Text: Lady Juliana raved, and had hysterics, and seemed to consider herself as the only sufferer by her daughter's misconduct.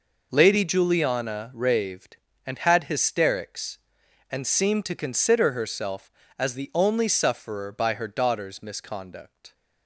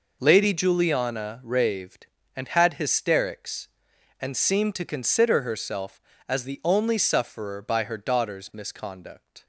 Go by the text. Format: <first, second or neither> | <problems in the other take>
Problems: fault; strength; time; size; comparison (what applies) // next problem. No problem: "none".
neither | none